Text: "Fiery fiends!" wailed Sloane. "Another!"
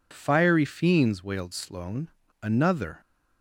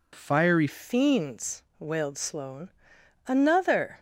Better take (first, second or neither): first